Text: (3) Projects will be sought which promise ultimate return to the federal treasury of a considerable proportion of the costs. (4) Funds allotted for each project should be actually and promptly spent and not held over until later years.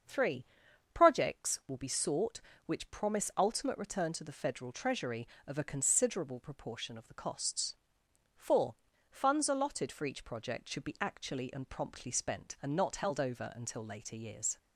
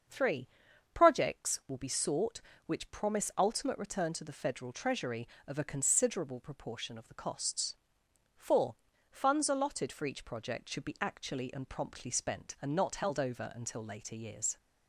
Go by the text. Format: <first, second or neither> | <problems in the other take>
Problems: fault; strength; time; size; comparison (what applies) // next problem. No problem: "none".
neither | starts louder than the rest; the same in both